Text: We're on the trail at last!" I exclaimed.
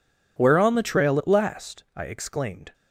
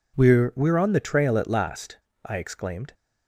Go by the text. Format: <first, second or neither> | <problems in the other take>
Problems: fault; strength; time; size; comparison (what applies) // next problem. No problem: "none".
first | says "We're" twice; at 0.5 s